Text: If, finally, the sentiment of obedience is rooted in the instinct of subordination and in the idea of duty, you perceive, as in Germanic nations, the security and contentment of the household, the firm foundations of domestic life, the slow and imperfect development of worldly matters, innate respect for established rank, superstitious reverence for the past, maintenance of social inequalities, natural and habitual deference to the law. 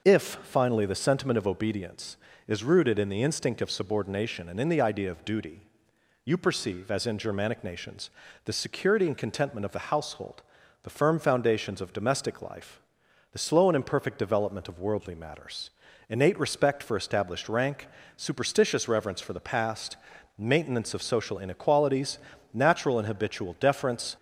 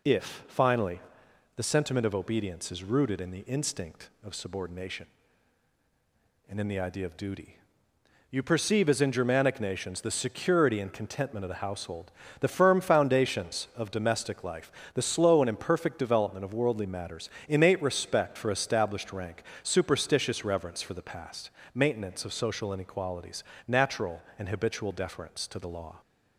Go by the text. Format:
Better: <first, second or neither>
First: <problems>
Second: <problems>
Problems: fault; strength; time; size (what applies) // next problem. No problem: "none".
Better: second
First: stops before "to the law"; at 24.1 s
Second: none